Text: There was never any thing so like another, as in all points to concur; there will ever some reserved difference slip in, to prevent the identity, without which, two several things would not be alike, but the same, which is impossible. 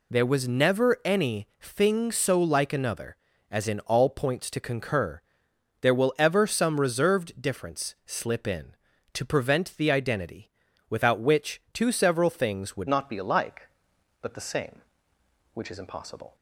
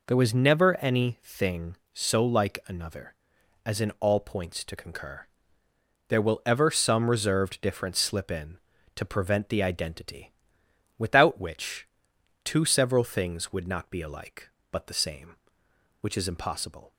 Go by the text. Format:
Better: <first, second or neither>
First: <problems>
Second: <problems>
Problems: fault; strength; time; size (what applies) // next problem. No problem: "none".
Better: second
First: changes voice at "not"; from 12.8 s on; 3.5 s long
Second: none